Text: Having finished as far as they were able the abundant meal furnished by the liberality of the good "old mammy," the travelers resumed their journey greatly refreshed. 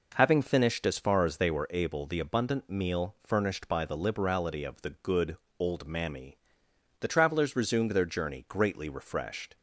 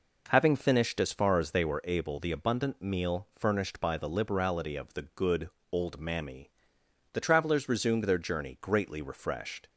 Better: neither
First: pauses between "good" and "old"; slight; at 5.3 s; 0.20 s long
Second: pauses between "good" and "old"; slight; at 5.5 s; 0.20 s long

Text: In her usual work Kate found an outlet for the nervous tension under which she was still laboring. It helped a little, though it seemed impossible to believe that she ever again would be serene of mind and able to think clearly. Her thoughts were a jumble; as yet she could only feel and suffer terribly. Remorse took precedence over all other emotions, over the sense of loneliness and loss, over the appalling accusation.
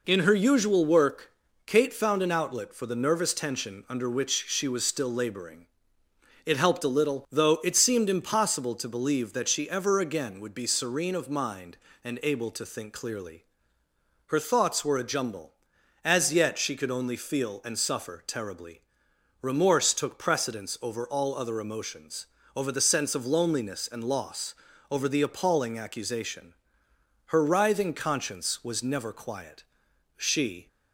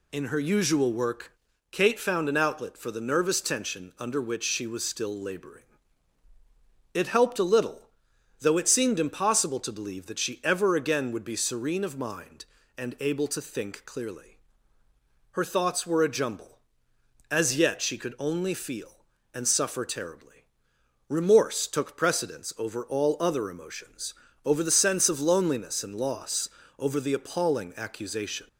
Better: second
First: pauses between "work" and "Kate"; slight; at 1.3 s; 0.34 s long // goes on to say "Her writhing conscience was never quiet She"; strong; from 27.2 s on; 3.4 s long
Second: pauses between "work" and "Kate"; at 1.3 s; 0.38 s long

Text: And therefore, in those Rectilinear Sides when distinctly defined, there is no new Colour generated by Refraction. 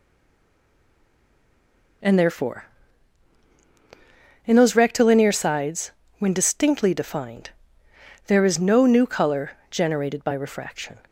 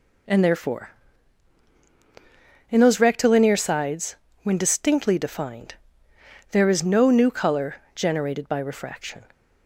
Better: second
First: stays silent before the first word; noticeable; until 2.0 s; 2.0 s long // pauses between "Sides" and "when"; slight; at 5.9 s; 0.28 s long // pauses between "Colour" and "generated"; slight; at 9.5 s; 0.20 s long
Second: pauses between "Sides" and "when"; slight; at 4.1 s; 0.28 s long // pauses between "Colour" and "generated"; slight; at 7.7 s; 0.20 s long

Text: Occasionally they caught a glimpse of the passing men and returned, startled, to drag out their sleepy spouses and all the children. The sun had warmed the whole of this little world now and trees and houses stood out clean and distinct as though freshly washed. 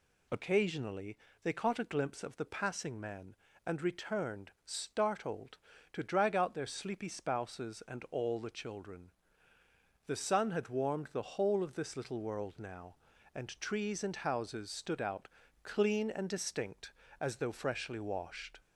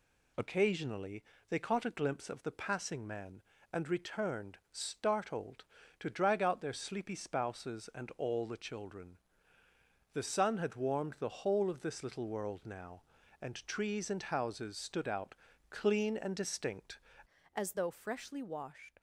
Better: first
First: pauses between "Occasionally" and "they"; slight; at 1.1 s; 0.26 s long // pauses between "out" and "clean"; slight; at 15.2 s; 0.36 s long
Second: pauses between "Occasionally" and "they"; slight; at 1.2 s; 0.26 s long // pauses between "out" and "clean"; slight; at 15.3 s; 0.36 s long // changes voice at "as"; from 17.5 s on; 1.5 s long

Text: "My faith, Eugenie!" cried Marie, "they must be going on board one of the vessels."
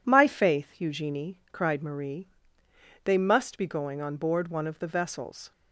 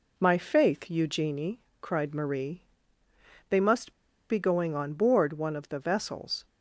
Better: first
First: none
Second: pauses between "must" and "be"; at 3.9 s; 0.37 s long

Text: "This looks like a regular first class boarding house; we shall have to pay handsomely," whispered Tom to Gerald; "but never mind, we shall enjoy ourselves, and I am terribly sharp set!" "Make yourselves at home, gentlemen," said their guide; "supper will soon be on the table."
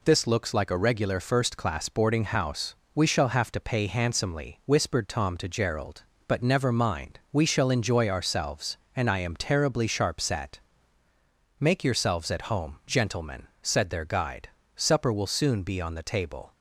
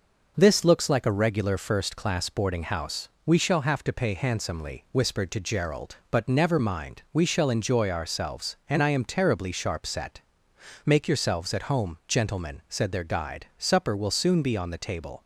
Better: first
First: none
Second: skips "Tom"; at 5.3 s

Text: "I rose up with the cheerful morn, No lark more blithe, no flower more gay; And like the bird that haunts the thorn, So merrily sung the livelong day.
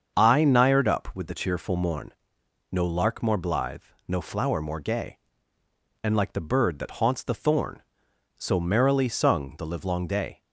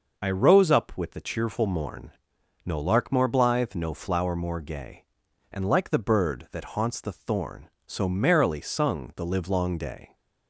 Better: second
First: starts louder than the rest; until 1.2 s; 7 dB // says "nired" for "rose"; at 0.4 s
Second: none

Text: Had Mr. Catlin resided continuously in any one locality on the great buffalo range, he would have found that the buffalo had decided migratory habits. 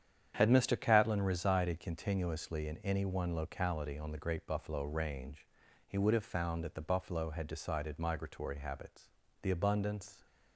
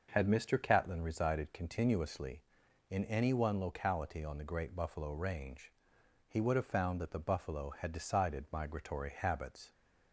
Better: second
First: starts louder than the rest; strong; until 1.3 s; 9 dB // goes on to say "The abundance"; noticeable; from 9.4 s on; 0.82 s long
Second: starts louder than the rest; noticeable; until 1.1 s; 6 dB

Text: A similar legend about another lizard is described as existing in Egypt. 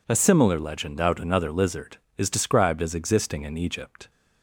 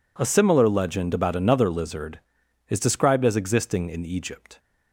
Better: second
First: says "out" for "about"; at 0.9 s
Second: none

